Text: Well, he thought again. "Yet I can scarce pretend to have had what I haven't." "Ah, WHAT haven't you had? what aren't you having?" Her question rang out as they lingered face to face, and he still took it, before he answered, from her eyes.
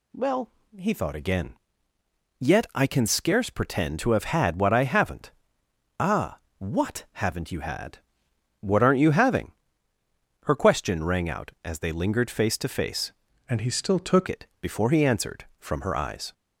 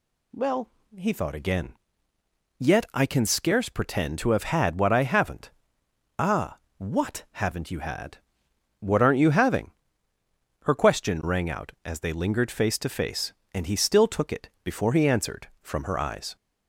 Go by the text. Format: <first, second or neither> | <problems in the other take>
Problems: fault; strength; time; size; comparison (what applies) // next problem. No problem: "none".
second | changes voice from "and" to "took"; from 13.4 to 14.2 s; 0.8 s long